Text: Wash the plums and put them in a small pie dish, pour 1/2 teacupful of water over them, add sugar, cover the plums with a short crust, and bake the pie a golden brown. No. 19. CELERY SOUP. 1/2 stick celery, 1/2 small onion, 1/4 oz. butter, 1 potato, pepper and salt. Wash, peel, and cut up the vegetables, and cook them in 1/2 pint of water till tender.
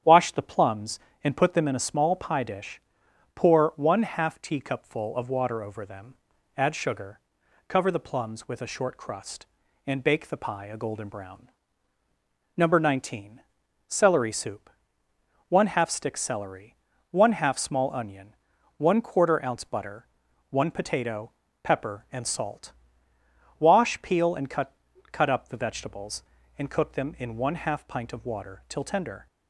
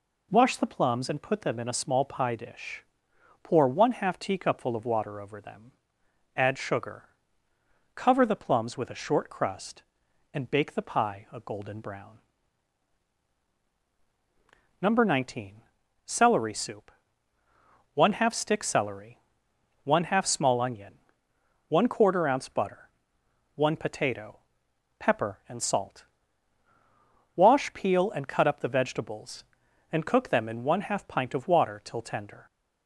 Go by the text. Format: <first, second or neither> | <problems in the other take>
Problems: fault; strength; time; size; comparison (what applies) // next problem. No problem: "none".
second | starts louder than the rest; strong; until 1.3 s; 9.5 dB // says "cut" twice; at 25.1 s